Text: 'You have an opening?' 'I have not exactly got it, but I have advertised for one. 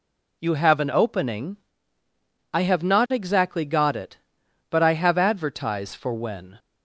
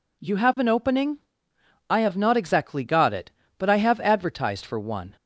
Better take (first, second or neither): second